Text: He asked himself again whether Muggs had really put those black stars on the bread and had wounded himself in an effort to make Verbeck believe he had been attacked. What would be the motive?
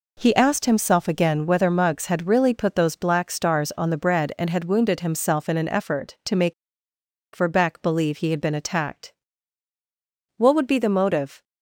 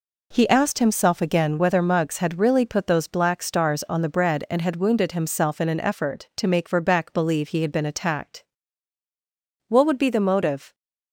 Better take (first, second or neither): second